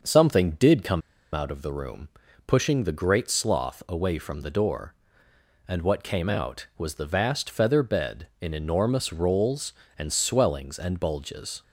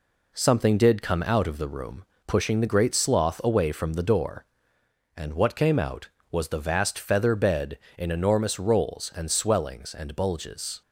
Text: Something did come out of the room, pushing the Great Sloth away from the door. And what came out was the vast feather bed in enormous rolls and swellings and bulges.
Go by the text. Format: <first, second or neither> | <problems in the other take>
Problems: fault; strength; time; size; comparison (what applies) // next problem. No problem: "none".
second | starts louder than the rest; until 1.3 s; 6 dB // pauses between "come" and "out"; slight; at 1.0 s; 0.33 s long